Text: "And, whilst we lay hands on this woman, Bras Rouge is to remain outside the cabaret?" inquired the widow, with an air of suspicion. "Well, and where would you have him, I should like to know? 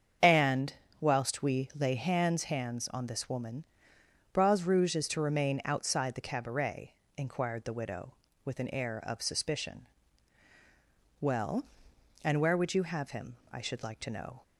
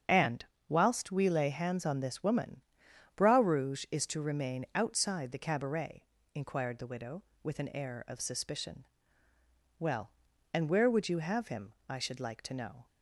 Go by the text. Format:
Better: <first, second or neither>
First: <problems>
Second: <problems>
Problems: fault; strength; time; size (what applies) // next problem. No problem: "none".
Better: second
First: starts louder than the rest; strong; until 1.4 s; 7.5 dB // says "hands" twice; at 2.4 s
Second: starts louder than the rest; strong; until 1.3 s; 7.5 dB